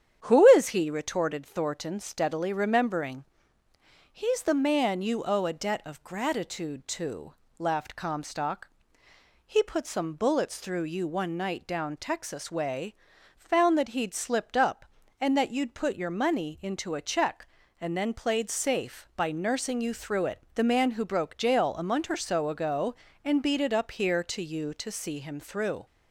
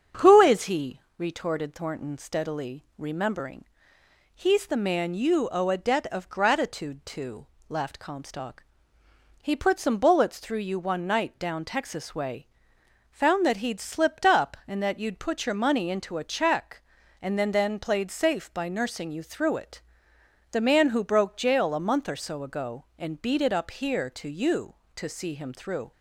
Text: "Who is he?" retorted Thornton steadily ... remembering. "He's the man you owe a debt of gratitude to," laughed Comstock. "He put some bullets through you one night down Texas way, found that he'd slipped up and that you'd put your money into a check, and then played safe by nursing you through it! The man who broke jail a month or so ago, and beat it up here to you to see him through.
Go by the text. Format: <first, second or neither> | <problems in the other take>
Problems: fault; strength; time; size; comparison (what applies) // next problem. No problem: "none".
first | starts louder than the rest; strong; until 1.3 s; 7.5 dB; strong in the first // says "then" twice; at 17.5 s